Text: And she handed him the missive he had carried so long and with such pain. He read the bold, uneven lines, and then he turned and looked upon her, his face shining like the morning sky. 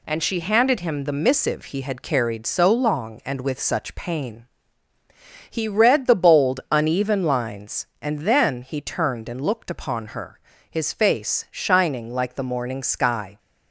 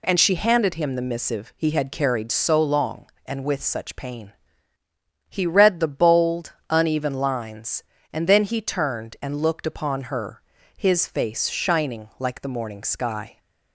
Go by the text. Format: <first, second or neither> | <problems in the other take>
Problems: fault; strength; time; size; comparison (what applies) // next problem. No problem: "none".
neither | none